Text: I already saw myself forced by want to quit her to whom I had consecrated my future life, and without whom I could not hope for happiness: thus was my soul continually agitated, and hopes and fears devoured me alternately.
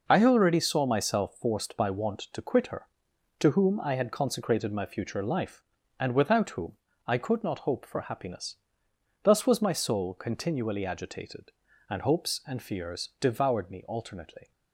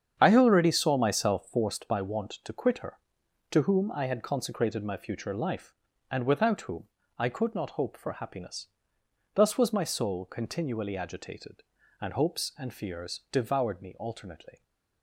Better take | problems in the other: first | starts louder than the rest; strong; until 1.8 s; 8 dB // pauses between "whom" and "I"; slight; at 6.8 s; 0.32 s long; slight in the first

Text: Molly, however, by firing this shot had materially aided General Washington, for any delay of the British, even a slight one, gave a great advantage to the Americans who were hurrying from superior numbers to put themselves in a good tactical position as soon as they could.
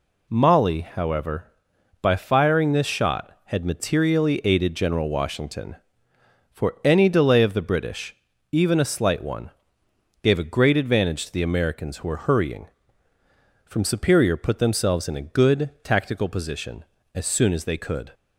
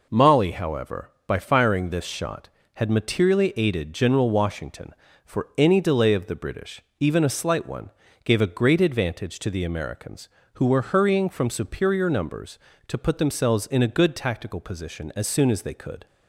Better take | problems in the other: second | skips "numbers to"; at 14.3 s

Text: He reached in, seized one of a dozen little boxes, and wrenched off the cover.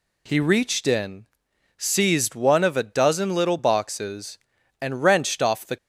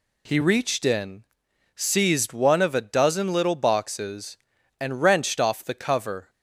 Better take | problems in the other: second | stops before "cover"; at 5.7 s

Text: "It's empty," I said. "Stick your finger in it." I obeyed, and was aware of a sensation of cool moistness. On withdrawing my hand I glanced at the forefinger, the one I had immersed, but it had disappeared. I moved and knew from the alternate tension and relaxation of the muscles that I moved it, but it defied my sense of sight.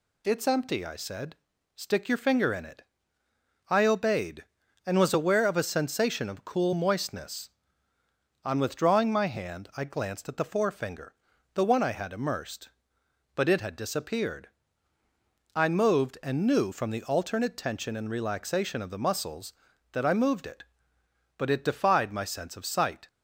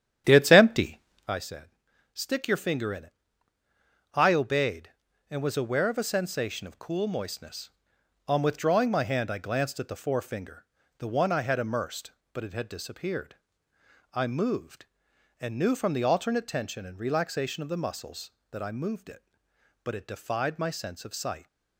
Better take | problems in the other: first | starts louder than the rest; strong; until 1.4 s; 10 dB

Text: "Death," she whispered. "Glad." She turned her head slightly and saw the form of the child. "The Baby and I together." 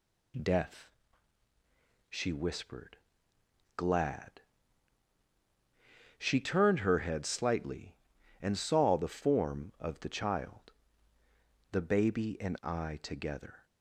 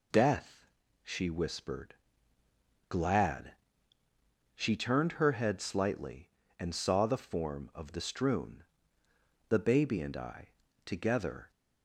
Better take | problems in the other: first | says "strewn" for "child"; at 7.9 s // pauses between "I" and "together"; at 10.4 s; 0.38 s long

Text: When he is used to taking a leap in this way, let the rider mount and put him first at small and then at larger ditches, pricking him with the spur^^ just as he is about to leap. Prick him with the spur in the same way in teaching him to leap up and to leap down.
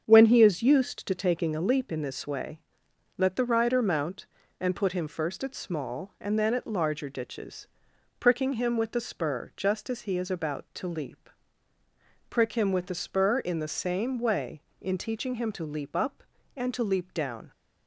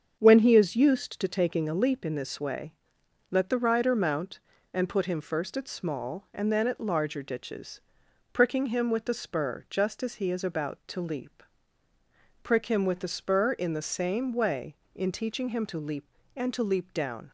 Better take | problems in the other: first | starts louder than the rest; strong; until 1.1 s; 7.5 dB; strong in the first // skips "up"; at 16.2 s

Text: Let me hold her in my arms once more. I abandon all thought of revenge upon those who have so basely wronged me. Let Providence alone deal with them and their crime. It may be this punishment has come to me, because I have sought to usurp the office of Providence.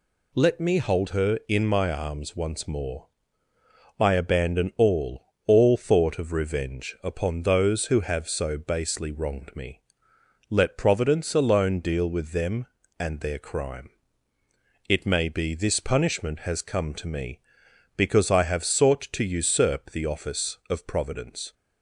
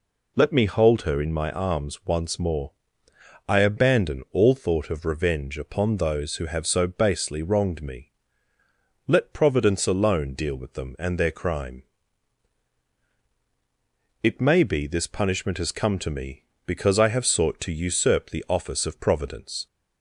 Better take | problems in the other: second | says "all" twice; at 5.4 s

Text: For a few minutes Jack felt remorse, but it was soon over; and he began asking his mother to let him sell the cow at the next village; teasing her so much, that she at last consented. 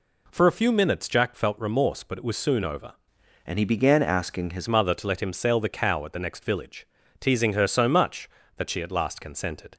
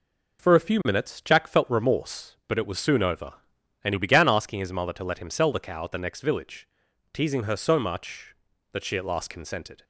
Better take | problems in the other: second | changes voice from "and" to "his"; from 3.4 to 4.6 s; 1.2 s long

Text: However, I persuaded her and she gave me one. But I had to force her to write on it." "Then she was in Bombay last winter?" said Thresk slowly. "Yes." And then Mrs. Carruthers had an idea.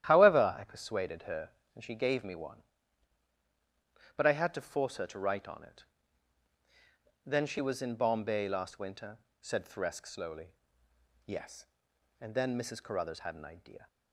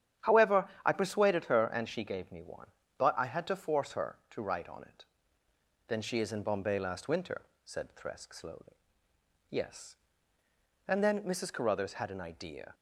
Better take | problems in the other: first | starts louder than the rest; strong; until 1.4 s; 10 dB; strong in the first // says "is" for "was"; at 6.1 s

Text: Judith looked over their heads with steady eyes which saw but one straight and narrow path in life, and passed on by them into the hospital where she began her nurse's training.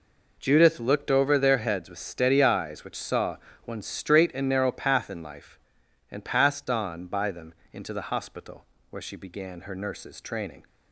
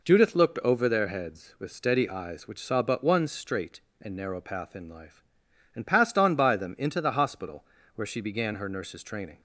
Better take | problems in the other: second | skips "but"; at 3.5 s // pauses between "them" and "into"; slight; at 7.5 s; 0.20 s long // pauses between "hospital" and "where"; slight; at 8.6 s; 0.24 s long; slight in the second

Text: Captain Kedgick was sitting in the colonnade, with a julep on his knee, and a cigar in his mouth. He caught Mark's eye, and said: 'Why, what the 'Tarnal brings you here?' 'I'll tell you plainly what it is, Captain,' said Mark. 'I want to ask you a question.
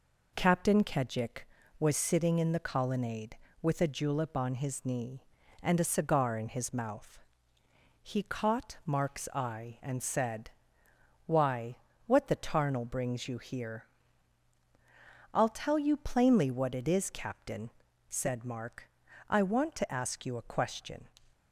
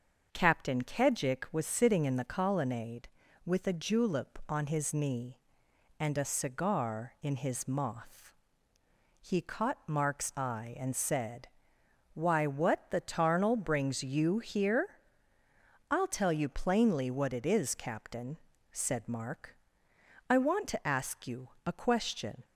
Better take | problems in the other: first | starts louder than the rest; until 1.3 s; 6.5 dB // says "moth" for "mouth"; at 7.6 s // pauses between "you" and "a"; slight; at 21.4 s; 0.18 s long

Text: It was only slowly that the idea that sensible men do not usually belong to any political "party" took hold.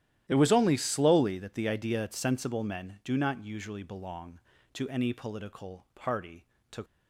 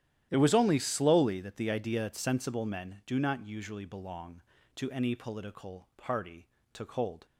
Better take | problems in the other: second | starts louder than the rest; strong; until 1.2 s; 13 dB; strong in the second // pauses between "party" and "took"; slight; at 6.4 s; 0.26 s long; slight in the second // stops before "hold"; at 6.8 s

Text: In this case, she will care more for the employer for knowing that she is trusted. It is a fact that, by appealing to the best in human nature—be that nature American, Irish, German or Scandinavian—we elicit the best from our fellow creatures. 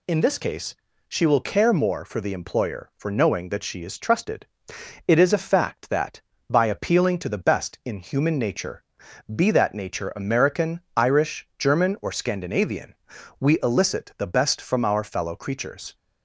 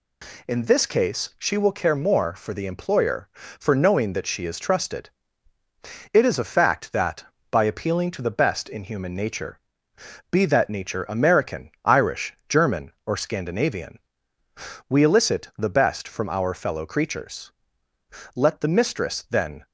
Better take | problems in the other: first | goes on to say "Let the mistress then"; noticeable; from 18.3 s on; 1.2 s long

